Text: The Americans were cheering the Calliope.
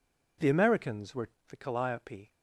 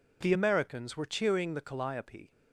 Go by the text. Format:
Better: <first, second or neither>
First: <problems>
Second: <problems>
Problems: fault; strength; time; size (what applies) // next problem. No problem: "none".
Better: second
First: skips "cheering"; at 1.3 s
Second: none